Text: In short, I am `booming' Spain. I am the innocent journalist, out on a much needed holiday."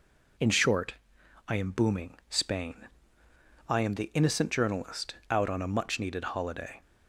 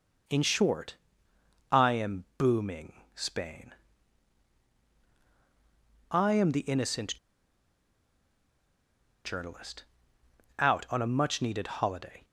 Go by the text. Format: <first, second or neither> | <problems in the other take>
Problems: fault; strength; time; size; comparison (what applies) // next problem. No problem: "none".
first | pauses between "innocent" and "journalist"; strong; at 7.1 s; 2.0 s long